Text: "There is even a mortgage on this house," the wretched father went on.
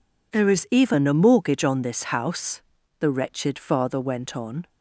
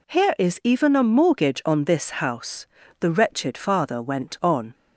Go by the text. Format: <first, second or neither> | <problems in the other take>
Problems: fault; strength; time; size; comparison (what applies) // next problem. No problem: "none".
first | says "Here" for "There"; at 0.0 s